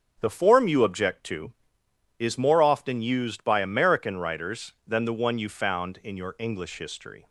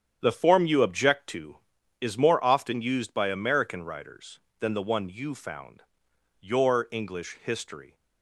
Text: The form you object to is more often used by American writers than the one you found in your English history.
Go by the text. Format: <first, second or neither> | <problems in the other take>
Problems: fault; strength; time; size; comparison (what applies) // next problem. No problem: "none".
first | starts louder than the rest; strong; until 1.2 s; 9 dB; strong in the first // skips "in"; at 6.1 s